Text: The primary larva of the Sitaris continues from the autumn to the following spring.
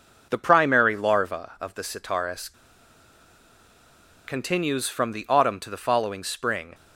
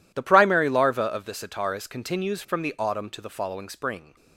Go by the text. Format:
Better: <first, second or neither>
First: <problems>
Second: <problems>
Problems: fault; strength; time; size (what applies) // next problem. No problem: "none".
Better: second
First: pauses between "Sitaris" and "continues"; strong; at 2.5 s; 1.7 s long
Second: none